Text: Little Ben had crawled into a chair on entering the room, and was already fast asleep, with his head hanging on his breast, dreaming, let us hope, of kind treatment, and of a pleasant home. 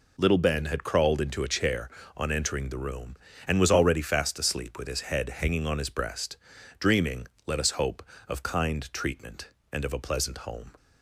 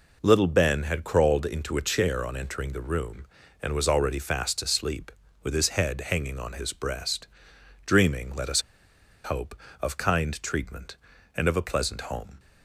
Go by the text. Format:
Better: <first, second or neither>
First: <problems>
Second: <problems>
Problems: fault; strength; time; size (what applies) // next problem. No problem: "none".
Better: first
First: none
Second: pauses between "us" and "hope"; noticeable; at 8.6 s; 0.63 s long